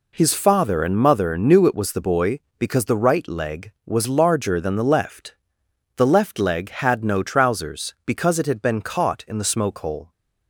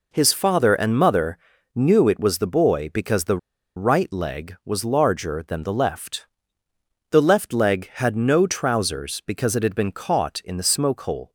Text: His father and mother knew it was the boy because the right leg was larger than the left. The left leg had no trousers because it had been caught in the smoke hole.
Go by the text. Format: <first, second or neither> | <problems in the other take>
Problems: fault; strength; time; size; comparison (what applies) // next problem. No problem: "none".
first | pauses between "mother" and "knew"; slight; at 1.3 s; 0.36 s long // pauses between "the" and "right"; at 3.3 s; 0.38 s long